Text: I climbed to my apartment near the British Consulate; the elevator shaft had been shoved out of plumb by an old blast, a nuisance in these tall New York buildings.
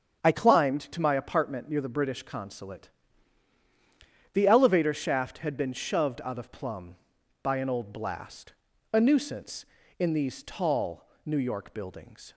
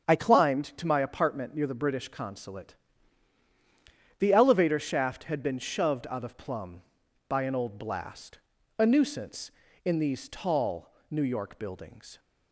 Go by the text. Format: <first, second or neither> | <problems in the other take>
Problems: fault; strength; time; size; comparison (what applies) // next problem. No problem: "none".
neither | starts louder than the rest; strong; the same in both // pauses between "tall" and "New"; slight; the same in both